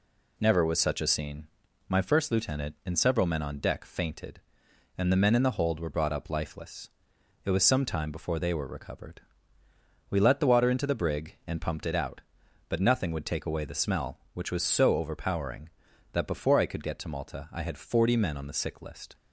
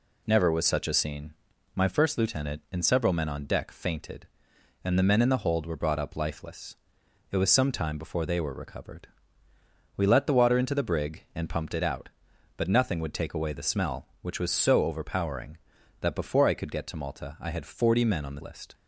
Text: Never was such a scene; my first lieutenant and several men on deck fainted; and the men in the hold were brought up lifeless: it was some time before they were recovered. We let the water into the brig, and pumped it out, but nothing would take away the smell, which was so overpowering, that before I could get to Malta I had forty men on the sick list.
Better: first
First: none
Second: skips "sick"; at 18.4 s

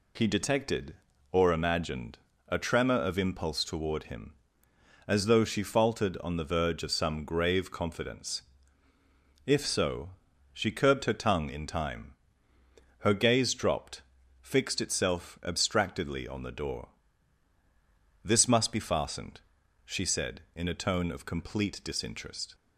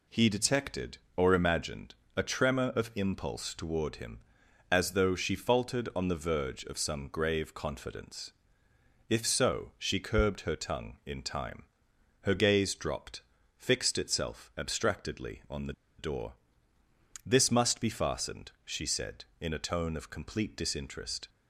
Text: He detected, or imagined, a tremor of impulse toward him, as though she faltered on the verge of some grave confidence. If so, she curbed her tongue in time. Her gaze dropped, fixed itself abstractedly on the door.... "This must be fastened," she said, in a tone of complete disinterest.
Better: first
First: none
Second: pauses between "the" and "door"; slight; at 15.7 s; 0.25 s long

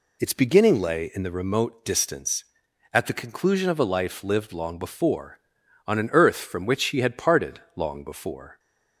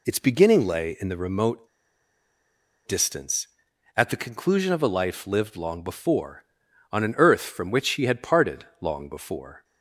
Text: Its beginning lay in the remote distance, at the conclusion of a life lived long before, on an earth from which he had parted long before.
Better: first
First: none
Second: pauses between "remote" and "distance"; at 1.6 s; 1.2 s long

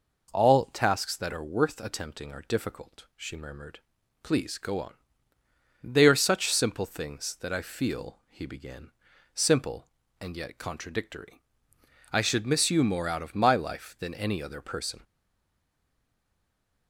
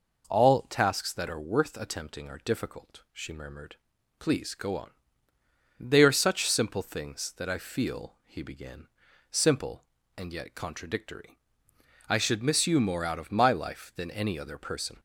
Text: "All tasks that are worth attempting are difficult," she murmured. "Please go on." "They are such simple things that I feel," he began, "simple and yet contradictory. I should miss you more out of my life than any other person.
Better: second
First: stays silent after the last word; noticeable; from 15.0 s on; 1.8 s long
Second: none

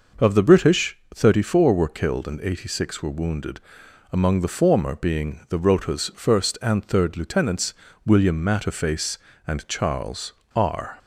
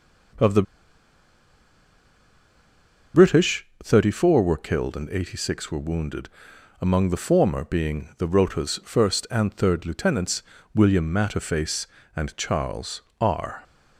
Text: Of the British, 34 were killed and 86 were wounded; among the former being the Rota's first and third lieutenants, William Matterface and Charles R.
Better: first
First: pauses between "Charles" and "R"; slight; at 10.3 s; 0.23 s long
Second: pauses between "the" and "British"; strong; at 0.6 s; 2.5 s long // pauses between "Charles" and "R"; slight; at 13.0 s; 0.20 s long

